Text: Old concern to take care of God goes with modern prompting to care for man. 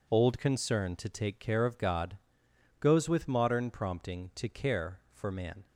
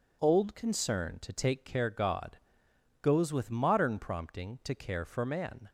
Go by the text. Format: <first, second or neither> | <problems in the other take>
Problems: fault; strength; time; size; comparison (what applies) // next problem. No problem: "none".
first | skips "of"; at 1.8 s // pauses between "God" and "goes"; noticeable; at 2.3 s; 0.62 s long; noticeable in the first